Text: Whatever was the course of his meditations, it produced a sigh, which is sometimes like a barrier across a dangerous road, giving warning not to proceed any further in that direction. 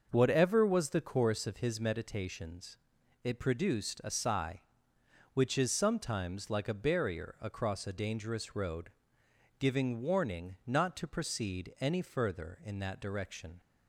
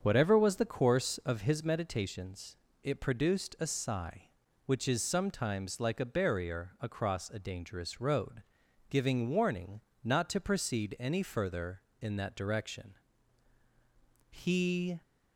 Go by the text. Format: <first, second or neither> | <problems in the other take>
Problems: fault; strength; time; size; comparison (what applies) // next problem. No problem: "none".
first | starts louder than the rest; strong; until 1.0 s; 7 dB; also in the first // pauses between "warning" and "not"; slight; at 9.7 s; 0.24 s long // goes on to say "He"; noticeable; from 14.2 s on; 0.72 s long